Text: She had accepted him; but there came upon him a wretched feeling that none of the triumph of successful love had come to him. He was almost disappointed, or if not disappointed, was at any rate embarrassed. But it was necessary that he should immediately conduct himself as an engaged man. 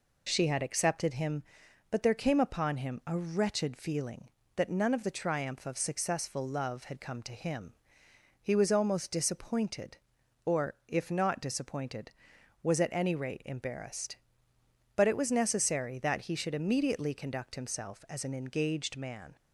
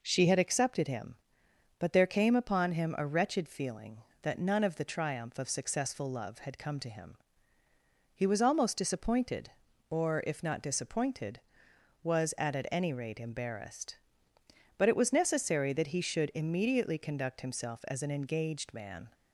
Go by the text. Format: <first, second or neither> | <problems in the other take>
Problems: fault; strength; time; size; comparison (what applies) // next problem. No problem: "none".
first | says "at" twice; at 12.5 s